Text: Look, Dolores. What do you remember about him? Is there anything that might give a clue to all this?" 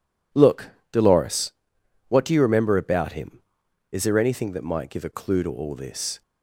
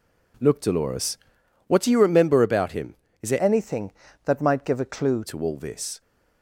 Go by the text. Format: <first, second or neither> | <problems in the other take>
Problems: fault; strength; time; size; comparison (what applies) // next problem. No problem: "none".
first | changes voice from "anything" to "clue"; from 3.4 to 5.2 s; 1.8 s long